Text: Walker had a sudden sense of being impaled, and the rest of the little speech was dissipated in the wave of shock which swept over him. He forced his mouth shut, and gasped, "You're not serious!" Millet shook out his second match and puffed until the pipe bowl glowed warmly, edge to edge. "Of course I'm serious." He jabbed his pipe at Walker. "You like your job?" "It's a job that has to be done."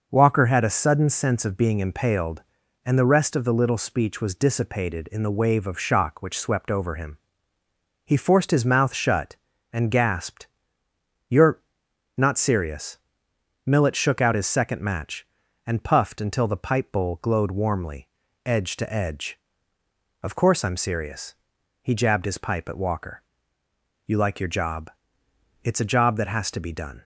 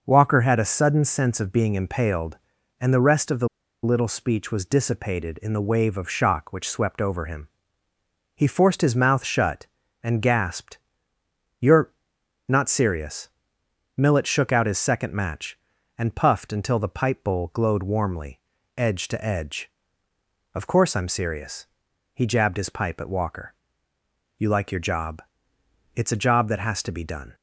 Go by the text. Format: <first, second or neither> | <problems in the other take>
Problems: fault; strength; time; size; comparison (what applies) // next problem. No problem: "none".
first | pauses between "the" and "little"; at 3.4 s; 0.36 s long // pauses between "You're" and "not"; noticeable; at 11.9 s; 0.56 s long; noticeable in the first